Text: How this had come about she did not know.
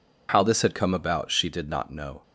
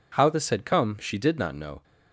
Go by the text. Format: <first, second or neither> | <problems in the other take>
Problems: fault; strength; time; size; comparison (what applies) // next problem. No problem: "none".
first | skips "about"; at 0.9 s